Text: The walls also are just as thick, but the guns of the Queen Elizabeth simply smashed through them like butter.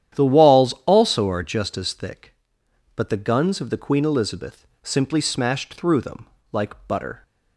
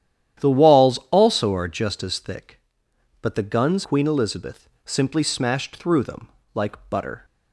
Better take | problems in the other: first | starts louder than the rest; strong; until 1.5 s; 11 dB; strong in the first // skips "of the"; at 3.8 s // pauses between "Elizabeth" and "simply"; slight; at 4.6 s; 0.16 s long; slight in the first // pauses between "them" and "like"; slight; at 6.2 s; 0.26 s long; slight in the first

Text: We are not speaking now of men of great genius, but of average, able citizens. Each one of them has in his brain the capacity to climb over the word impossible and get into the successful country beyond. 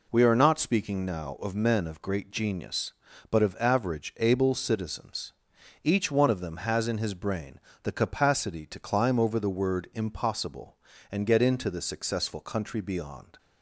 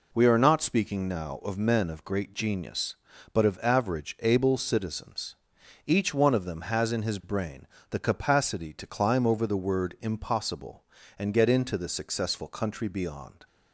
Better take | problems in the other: neither | pauses between "brain" and "the"; slight; the same in both

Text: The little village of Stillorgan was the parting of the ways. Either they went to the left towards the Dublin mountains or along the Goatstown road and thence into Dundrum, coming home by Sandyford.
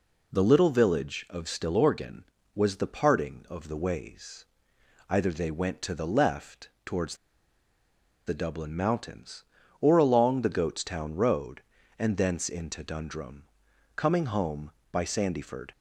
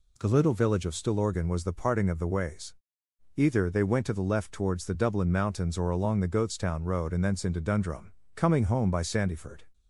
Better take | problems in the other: second | pauses between "left" and "towards"; slight; at 6.6 s; 0.16 s long // pauses between "towards" and "the"; at 7.1 s; 1.1 s long

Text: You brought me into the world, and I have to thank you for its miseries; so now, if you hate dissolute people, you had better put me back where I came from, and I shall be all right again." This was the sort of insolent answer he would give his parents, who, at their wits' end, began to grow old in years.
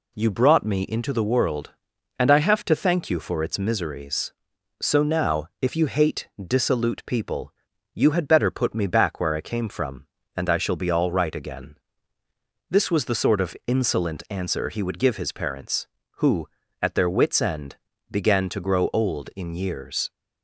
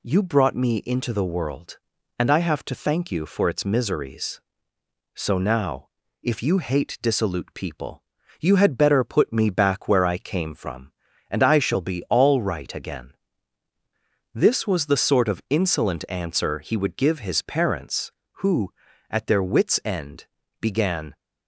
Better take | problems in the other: first | stops before "to grow old in years"; at 21.1 s

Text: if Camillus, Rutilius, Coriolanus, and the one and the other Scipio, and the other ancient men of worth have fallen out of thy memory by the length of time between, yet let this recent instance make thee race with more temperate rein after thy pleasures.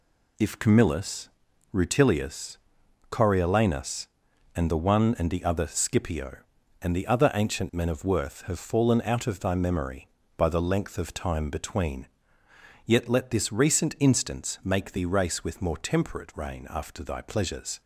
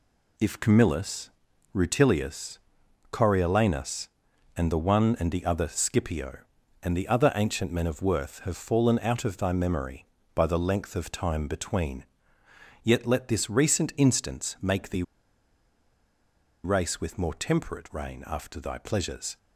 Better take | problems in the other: first | pauses between "thee" and "race"; strong; at 15.0 s; 1.6 s long

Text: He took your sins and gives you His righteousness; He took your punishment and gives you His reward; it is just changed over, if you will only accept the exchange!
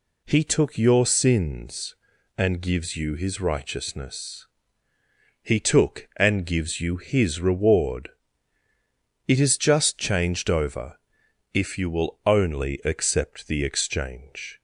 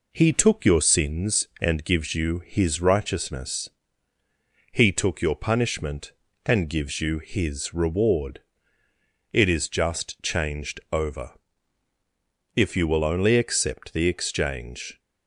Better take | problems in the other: second | skips "your punishment"; at 6.1 s

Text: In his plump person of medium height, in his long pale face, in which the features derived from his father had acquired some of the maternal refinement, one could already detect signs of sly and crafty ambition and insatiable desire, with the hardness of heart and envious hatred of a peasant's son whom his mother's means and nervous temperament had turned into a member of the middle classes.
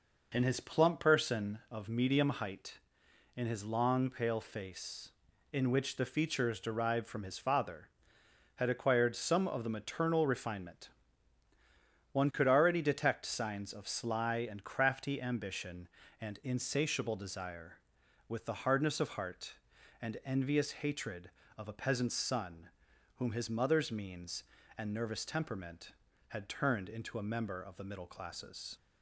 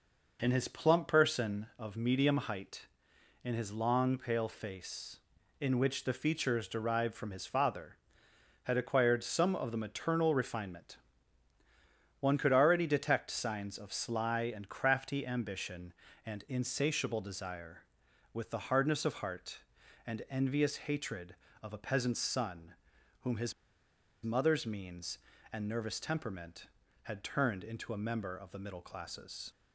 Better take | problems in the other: first | pauses between "son" and "whom"; noticeable; at 22.7 s; 0.48 s long; noticeable in the first // pauses between "his" and "mother's"; noticeable; at 23.5 s; 0.71 s long

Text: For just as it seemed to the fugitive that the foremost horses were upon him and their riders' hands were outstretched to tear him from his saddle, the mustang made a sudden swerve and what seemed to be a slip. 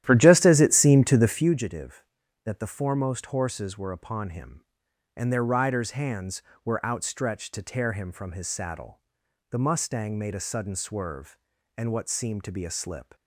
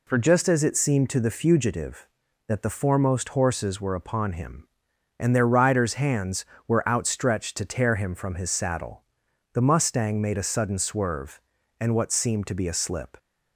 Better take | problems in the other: second | starts louder than the rest; strong; until 1.5 s; 12 dB

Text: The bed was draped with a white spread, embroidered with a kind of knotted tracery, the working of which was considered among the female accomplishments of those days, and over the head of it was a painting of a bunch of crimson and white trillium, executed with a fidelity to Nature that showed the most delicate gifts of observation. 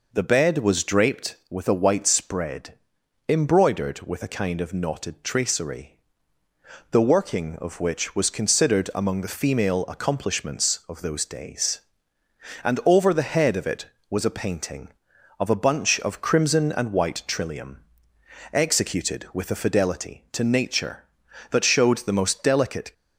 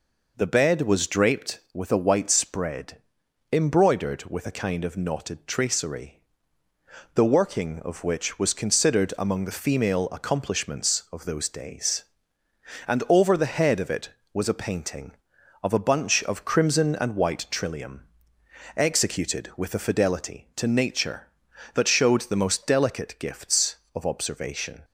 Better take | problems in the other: second | stops before "gifts of observation"; at 22.9 s

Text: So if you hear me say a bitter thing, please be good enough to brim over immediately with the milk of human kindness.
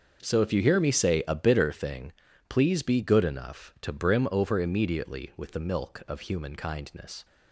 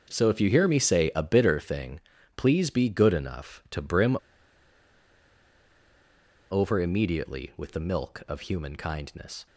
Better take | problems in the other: first | starts louder than the rest; until 1.1 s; 6.5 dB; also in the first // pauses between "brim" and "over"; strong; at 4.1 s; 2.3 s long

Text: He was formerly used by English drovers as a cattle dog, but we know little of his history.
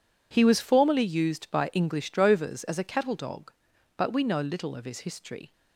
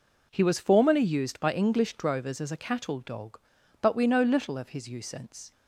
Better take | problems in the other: first | says "usance" for "history"; at 4.8 s

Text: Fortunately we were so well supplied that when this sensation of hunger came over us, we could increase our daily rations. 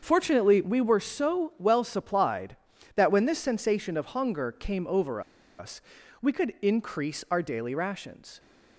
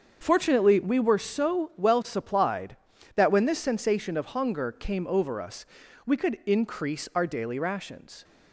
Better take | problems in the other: second | starts louder than the rest; until 1.0 s; 7 dB; also in the second // pauses between "over" and "us"; at 5.2 s; 0.37 s long

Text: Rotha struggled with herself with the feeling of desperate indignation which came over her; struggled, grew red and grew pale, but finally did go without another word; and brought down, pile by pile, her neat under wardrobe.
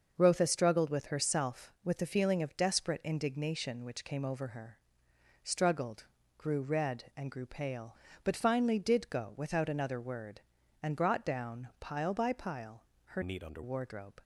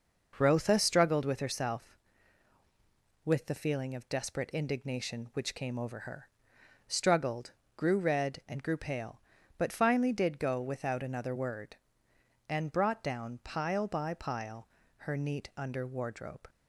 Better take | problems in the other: second | starts louder than the rest; until 1.1 s; 6 dB // changes voice from "neat" to "under"; from 13.2 to 13.6 s; 0.4 s long

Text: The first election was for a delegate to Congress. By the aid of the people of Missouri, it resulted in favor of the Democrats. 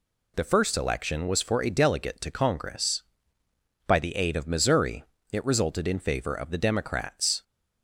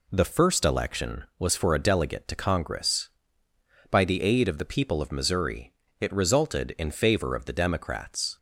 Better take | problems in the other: second | skips "the people of"; at 4.4 s

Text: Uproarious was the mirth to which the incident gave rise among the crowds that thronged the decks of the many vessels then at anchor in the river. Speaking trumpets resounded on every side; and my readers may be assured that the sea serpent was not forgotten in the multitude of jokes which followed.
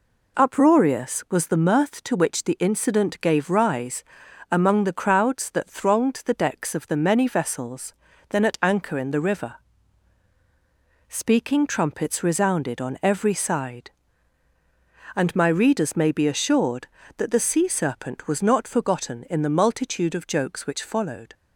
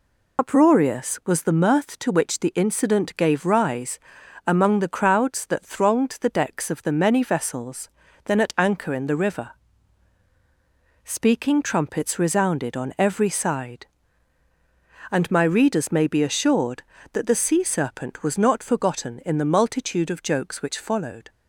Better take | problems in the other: first | loses the start of "Uproarious"; at 0.3 s; 70 ms // pauses between "rise" and "among"; noticeable; at 3.9 s; 0.48 s long; noticeable in the first // pauses between "vessels" and "then"; slight; at 7.8 s; 0.36 s long; slight in the first

